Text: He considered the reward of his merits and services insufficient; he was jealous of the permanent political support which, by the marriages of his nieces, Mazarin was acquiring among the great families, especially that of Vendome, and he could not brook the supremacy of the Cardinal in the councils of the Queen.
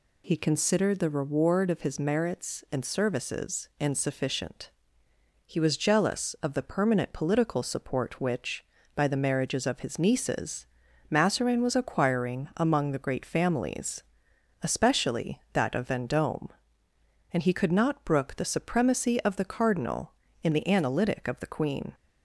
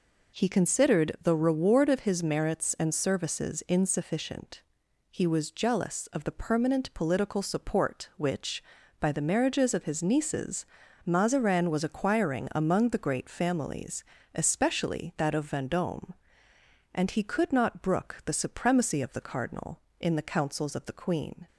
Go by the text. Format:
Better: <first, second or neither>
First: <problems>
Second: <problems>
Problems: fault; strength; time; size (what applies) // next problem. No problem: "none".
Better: second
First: says "analytic" for "councils"; at 20.6 s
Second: none